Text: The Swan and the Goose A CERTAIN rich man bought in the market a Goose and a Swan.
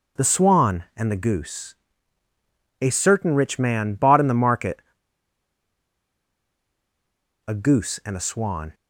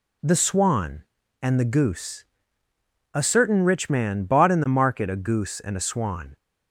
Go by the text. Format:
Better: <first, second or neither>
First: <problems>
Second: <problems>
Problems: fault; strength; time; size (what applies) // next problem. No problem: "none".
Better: second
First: pauses between "Goose" and "A"; at 1.7 s; 1.0 s long // pauses between "market" and "a"; strong; at 4.8 s; 2.6 s long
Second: pauses between "Goose" and "A"; noticeable; at 2.2 s; 0.90 s long